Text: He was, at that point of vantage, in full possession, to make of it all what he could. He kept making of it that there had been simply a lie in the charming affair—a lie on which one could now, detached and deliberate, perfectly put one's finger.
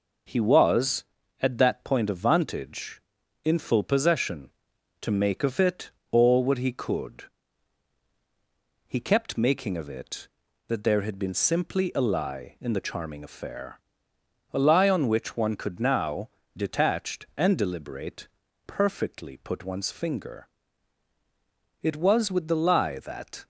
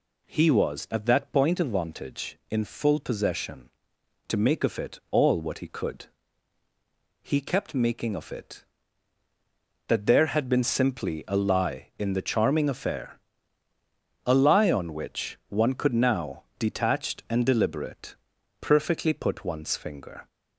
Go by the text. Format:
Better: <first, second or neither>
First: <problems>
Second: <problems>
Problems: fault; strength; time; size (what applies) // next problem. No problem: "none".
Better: second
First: pauses between "it" and "all"; slight; at 5.8 s; 0.22 s long // goes on to say "It was with the lie that"; from 21.8 s on; 1.6 s long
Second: none